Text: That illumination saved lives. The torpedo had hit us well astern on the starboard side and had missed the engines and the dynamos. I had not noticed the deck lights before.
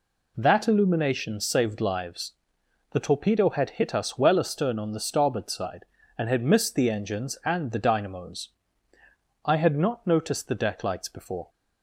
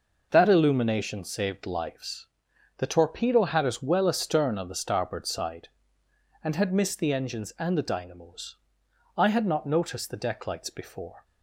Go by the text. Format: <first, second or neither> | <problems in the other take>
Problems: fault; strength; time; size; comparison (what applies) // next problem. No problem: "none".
first | skips "hit"; at 3.6 s